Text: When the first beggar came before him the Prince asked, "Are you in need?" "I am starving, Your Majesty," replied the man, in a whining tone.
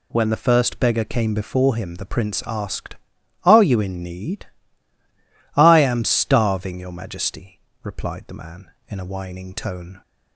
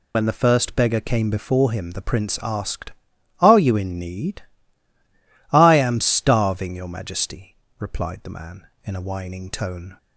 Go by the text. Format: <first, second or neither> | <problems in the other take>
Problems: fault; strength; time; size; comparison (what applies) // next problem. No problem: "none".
first | loses the start of "When"; at 0.1 s; 75 ms